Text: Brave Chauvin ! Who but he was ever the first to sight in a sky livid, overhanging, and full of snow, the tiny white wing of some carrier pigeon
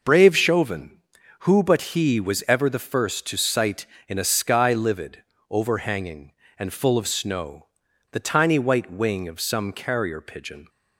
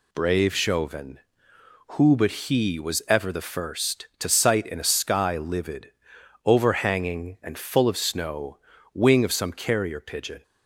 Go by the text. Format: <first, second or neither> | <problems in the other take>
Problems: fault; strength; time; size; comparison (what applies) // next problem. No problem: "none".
first | skips "the tiny white"; at 8.7 s